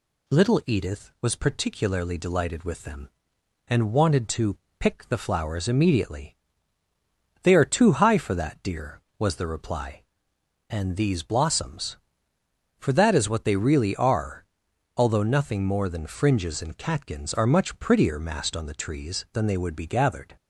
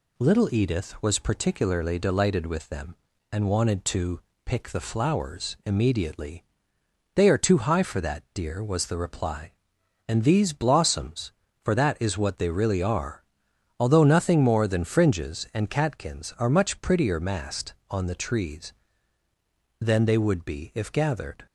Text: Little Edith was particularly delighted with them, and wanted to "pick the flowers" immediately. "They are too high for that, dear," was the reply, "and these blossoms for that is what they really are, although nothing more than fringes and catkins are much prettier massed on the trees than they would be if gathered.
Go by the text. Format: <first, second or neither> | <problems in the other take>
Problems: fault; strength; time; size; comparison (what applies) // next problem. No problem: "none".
second | pauses between "to" and "pick"; slight; at 4.5 s; 0.22 s long; slight in the second // skips "if"; at 19.8 s